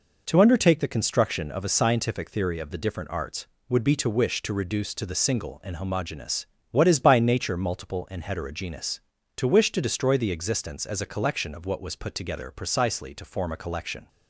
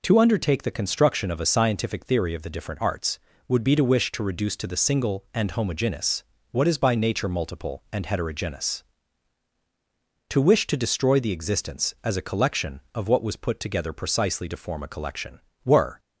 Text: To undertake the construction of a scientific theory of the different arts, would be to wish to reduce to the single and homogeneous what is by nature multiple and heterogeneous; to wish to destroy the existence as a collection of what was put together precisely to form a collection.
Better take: first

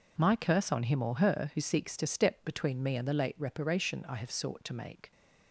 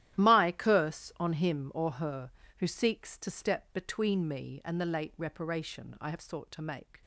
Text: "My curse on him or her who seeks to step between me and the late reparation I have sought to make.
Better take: first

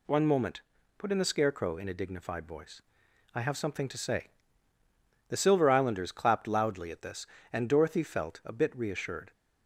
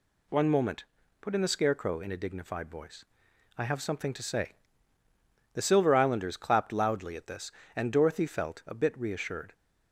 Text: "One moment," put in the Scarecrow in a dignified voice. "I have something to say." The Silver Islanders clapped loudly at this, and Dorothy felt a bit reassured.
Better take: neither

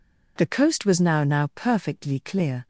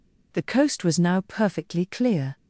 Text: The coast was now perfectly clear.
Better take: second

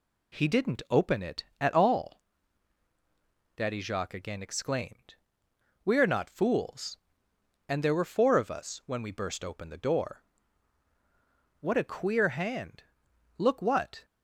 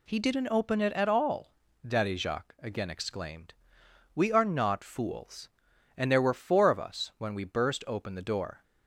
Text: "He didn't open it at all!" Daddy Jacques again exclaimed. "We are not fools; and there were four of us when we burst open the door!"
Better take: second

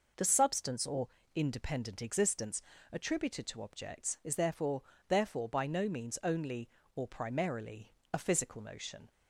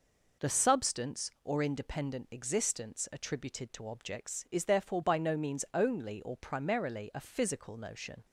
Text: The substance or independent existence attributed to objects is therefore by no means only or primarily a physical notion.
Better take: second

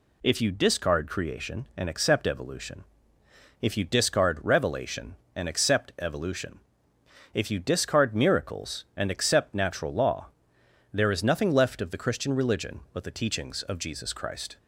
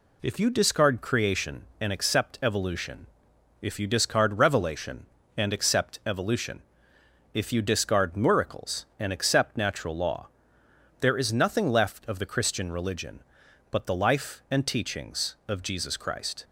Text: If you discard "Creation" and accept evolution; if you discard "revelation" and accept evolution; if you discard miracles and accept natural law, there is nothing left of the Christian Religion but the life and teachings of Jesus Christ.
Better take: second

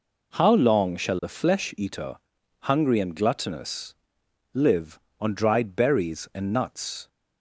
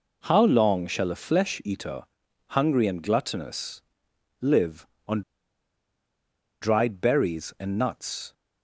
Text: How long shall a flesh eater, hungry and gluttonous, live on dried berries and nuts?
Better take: first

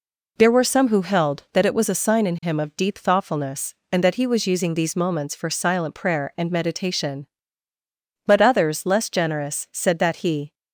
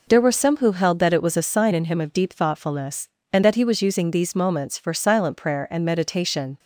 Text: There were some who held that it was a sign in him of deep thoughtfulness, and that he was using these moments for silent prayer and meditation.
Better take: second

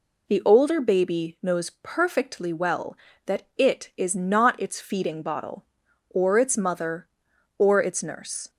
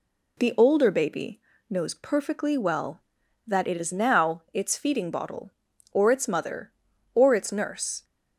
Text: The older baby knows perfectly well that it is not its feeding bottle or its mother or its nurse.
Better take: first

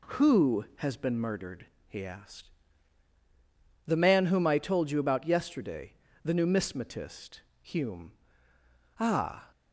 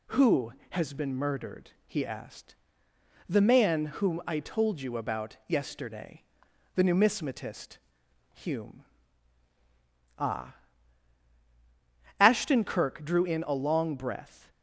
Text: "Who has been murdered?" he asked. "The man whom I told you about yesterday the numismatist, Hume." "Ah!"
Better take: first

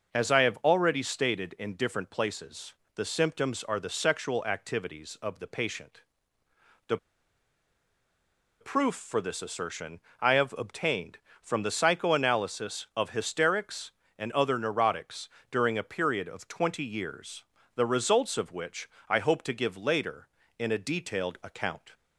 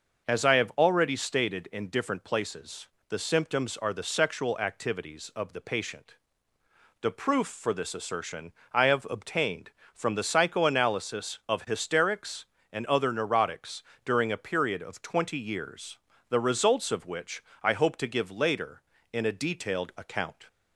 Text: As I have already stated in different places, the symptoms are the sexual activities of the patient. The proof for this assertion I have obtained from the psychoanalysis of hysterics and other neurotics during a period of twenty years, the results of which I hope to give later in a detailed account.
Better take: second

